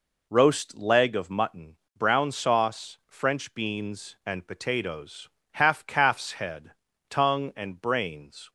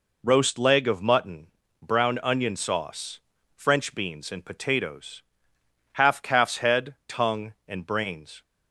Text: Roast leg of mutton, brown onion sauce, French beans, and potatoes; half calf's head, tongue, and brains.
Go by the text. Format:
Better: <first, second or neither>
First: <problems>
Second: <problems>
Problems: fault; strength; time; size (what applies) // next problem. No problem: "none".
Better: second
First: skips "onion"; at 2.3 s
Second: none